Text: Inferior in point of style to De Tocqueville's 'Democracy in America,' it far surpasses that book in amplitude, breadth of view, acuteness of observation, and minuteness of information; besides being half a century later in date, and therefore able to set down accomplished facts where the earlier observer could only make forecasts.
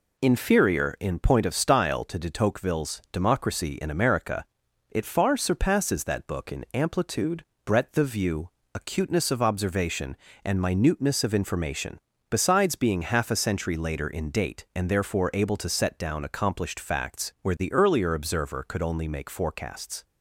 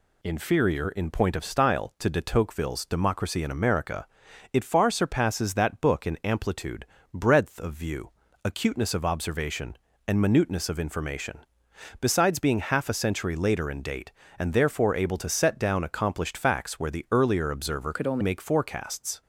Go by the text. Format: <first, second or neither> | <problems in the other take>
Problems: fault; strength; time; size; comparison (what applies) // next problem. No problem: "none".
first | changes voice from "could" to "only"; from 17.9 to 18.2 s; 0.3 s long